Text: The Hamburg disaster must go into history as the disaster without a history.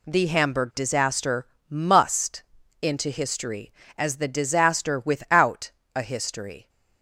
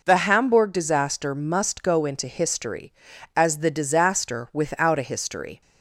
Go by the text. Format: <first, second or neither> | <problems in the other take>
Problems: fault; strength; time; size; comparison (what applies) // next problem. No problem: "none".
second | pauses between "disaster" and "must"; slight; at 1.4 s; 0.22 s long // skips "go"; at 2.6 s // pauses between "without" and "a"; slight; at 5.7 s; 0.24 s long